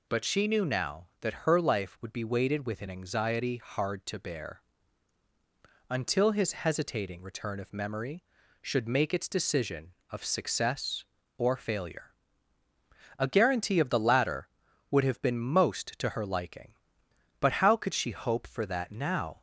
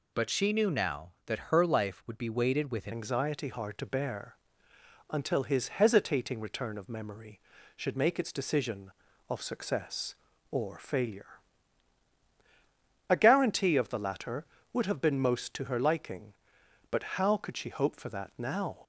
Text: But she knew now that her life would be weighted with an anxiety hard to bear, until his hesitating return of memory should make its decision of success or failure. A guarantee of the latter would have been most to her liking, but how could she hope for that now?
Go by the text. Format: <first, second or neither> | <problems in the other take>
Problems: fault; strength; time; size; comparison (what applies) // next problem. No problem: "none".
first | changes voice at "anxiety"; from 2.9 s on; 15.8 s long